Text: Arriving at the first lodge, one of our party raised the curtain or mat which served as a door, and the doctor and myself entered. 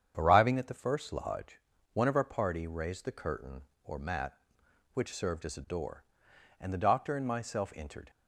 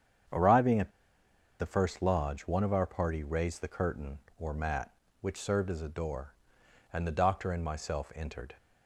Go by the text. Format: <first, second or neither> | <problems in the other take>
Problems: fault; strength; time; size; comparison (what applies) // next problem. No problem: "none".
first | starts louder than the rest; strong; until 2.0 s; 8 dB; strong in the first // pauses between "at" and "the"; noticeable; at 0.8 s; 0.69 s long